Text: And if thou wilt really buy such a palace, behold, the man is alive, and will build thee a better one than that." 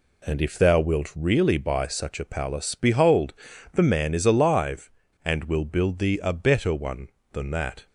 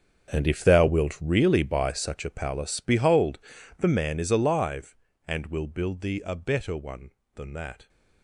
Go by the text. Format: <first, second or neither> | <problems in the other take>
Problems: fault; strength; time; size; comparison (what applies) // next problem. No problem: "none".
first | gets quieter; strong; throughout; 16 dB